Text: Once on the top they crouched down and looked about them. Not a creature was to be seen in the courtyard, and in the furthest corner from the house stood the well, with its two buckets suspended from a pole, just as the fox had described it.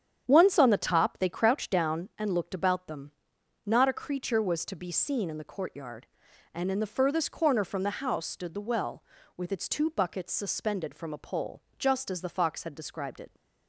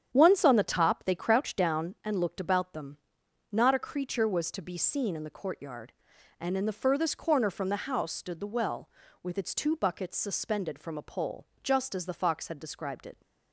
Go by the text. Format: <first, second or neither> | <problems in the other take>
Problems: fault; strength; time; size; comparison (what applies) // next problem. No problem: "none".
neither | starts louder than the rest; strong; the same in both